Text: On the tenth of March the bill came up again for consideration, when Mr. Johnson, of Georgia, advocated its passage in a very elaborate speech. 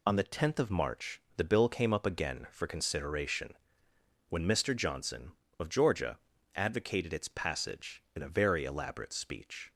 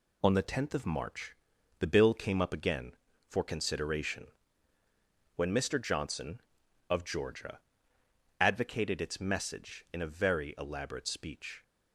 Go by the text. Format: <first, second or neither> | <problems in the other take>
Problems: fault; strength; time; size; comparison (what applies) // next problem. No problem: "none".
first | pauses between "March" and "the"; at 1.3 s; 0.44 s long; slight in the first // says "message" for "passage"; at 9.1 s